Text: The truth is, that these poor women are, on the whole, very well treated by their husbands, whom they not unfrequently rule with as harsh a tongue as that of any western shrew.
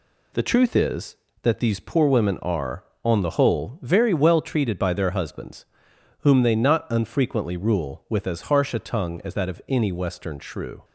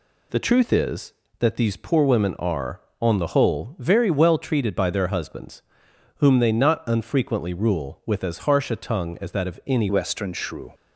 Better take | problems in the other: first | changes voice at "western"; from 9.8 s on; 0.9 s long

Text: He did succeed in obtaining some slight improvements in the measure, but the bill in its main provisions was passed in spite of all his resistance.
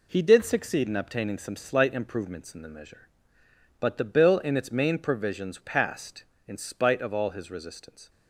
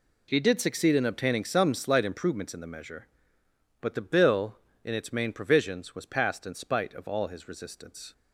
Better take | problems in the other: second | skips "was"; at 5.6 s

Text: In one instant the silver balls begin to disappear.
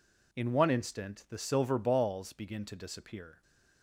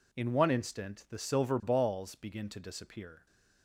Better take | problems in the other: neither | none

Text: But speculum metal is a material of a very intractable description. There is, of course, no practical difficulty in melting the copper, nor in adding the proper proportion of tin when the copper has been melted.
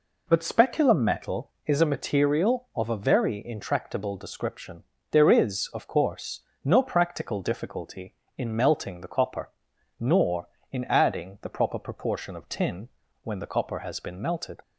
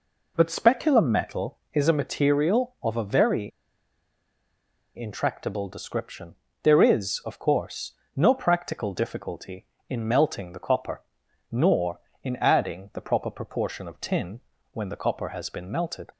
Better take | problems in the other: first | pauses between "very" and "intractable"; strong; at 3.5 s; 1.4 s long // pauses between "tin" and "when"; slight; at 14.4 s; 0.32 s long; slight in the first

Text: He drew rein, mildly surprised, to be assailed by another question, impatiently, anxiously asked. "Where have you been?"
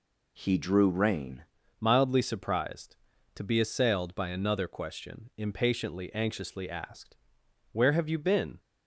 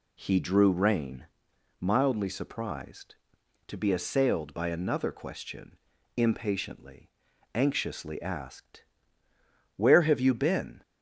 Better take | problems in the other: second | changes voice at "mildly"; from 1.8 s on; 6.7 s long

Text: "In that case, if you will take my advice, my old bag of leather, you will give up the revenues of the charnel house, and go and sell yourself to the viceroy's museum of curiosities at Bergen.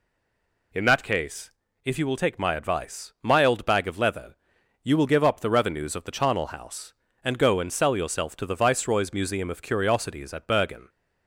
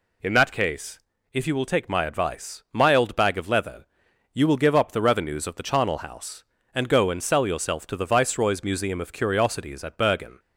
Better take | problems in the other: second | stays silent before the first word; slight; until 0.7 s; 0.7 s long

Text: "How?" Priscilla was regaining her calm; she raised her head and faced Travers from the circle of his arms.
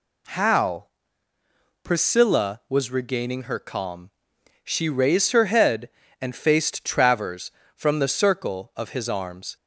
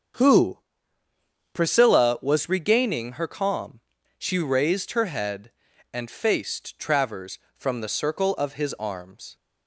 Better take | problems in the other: first | starts louder than the rest; strong; until 2.1 s; 7 dB // says "Who" for "How"; at 0.1 s

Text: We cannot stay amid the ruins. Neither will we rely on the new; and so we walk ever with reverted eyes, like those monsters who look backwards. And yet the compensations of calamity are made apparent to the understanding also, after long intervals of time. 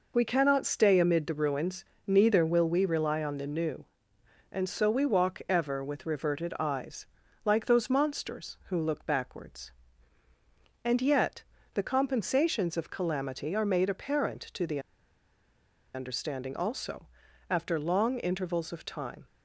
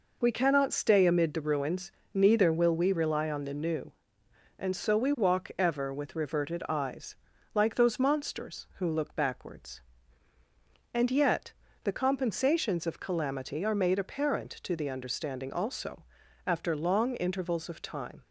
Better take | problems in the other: second | pauses between "yet" and "the"; slight; at 11.4 s; 0.30 s long; slight in the second // pauses between "the" and "understanding"; at 14.7 s; 1.1 s long

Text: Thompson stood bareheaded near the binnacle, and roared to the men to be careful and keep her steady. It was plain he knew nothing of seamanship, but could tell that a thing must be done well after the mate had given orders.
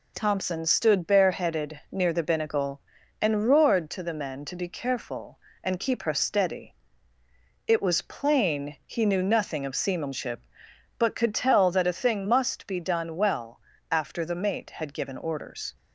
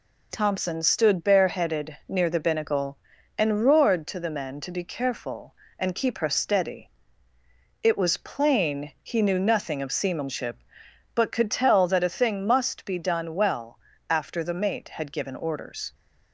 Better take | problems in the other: neither | pauses between "well" and "after"; slight; the same in both

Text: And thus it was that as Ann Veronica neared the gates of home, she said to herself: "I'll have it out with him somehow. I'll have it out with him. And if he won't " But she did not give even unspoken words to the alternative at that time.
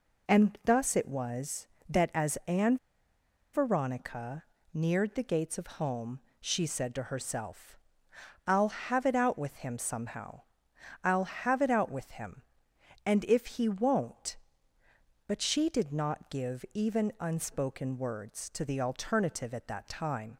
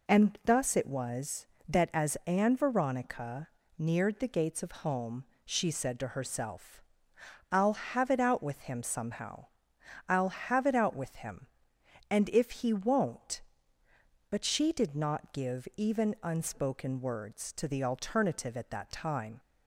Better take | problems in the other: second | pauses between "Ann" and "Veronica"; noticeable; at 2.7 s; 0.77 s long // pauses between "Veronica" and "neared"; slight; at 4.4 s; 0.28 s long; slight in the second

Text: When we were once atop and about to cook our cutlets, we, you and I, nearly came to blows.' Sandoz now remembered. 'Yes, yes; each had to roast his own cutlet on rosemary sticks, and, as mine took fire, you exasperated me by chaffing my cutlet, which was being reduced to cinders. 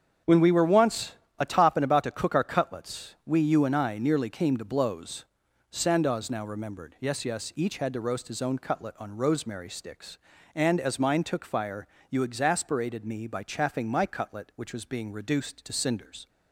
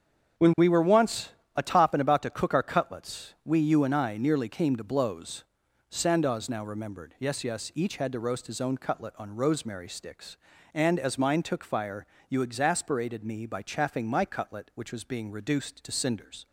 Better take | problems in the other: neither | starts louder than the rest; strong; the same in both // pauses between "once" and "atop"; slight; the same in both

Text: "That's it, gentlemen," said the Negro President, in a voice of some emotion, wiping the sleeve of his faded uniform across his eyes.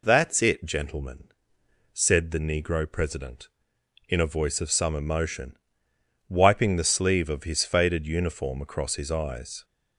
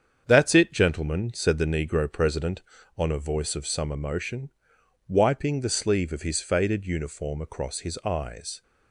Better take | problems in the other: first | starts louder than the rest; strong; until 1.2 s; 7.5 dB // says "on" for "in"; at 2.9 s

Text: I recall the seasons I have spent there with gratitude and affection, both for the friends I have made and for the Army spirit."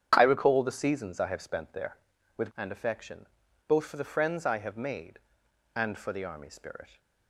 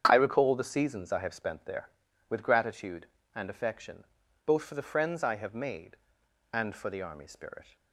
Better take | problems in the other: second | starts louder than the rest; strong; until 1.1 s; 8 dB; strong in the second // skips "gratitude"; at 2.5 s

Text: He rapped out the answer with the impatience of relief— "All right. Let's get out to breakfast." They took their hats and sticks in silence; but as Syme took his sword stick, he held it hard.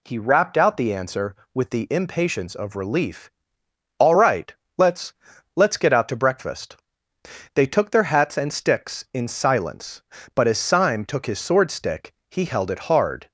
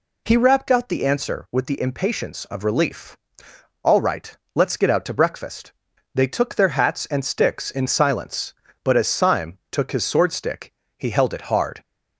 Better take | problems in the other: second | says "Let's" twice; at 5.5 s

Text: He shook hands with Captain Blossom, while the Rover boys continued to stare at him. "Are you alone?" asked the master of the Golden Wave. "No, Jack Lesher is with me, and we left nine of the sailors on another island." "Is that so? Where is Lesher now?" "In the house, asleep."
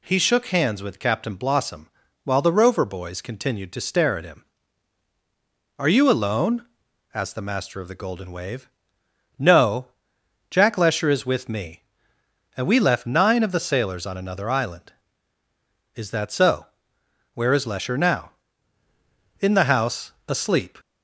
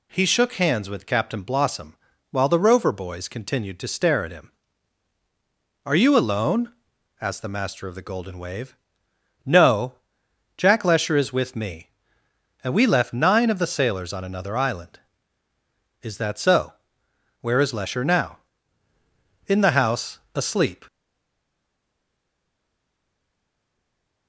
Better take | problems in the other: first | stays silent after the last word; strong; from 20.8 s on; 3.4 s long

